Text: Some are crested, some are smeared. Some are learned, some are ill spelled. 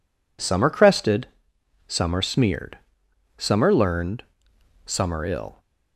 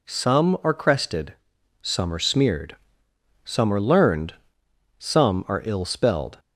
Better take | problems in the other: second | stops before "spelled"; at 5.5 s

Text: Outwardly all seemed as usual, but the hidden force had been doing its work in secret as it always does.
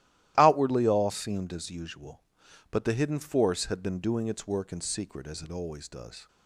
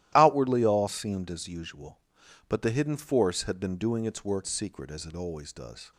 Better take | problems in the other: first | starts louder than the rest; strong; until 1.1 s; 14 dB; strong in the first // skips "in"; at 4.4 s

